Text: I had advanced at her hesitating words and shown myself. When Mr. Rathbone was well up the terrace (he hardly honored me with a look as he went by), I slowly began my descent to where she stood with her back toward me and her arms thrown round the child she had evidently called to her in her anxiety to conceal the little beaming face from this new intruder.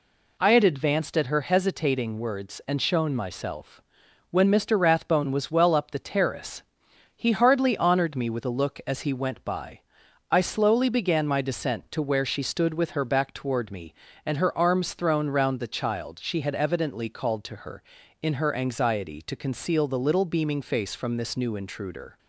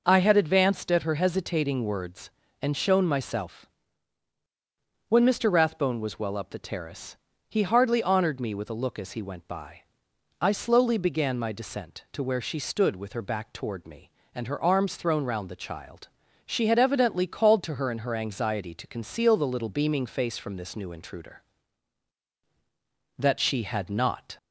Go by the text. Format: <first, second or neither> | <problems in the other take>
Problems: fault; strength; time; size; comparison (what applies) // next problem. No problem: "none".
first | pauses between "child" and "she"; at 16.0 s; 0.38 s long // goes on to say "That she had not"; noticeable; from 23.1 s on; 1.2 s long